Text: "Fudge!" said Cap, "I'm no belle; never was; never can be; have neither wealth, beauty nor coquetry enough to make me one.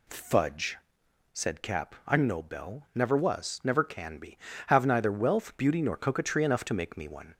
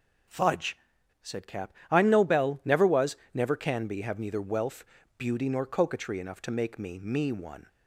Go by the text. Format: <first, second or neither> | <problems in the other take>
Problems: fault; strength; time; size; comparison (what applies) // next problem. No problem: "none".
first | says "me" twice; at 6.9 s